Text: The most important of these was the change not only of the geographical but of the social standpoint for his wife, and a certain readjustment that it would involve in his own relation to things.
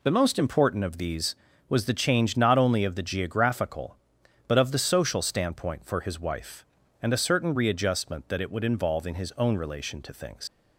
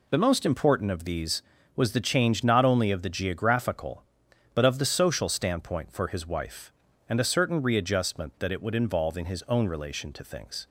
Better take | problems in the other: second | leaves "things" unfinished; at 10.4 s; 80 ms

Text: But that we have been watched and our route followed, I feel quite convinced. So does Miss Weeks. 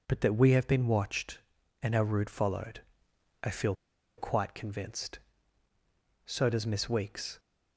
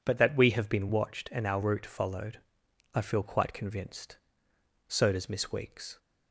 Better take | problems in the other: second | pauses between "feel" and "quite"; at 3.7 s; 0.42 s long

